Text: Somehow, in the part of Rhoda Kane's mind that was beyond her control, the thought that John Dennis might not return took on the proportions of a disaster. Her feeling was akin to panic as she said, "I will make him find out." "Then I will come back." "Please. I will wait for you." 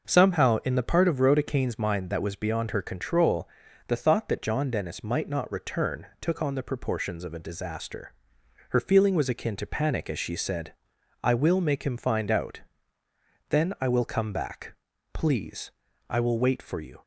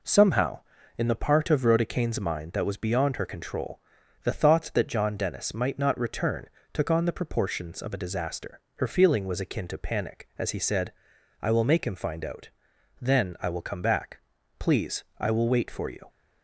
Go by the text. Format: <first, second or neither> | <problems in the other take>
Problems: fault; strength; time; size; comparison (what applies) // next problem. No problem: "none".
first | pauses between "return" and "took"; slight; at 6.4 s; 0.24 s long // says "he" for "she"; at 10.5 s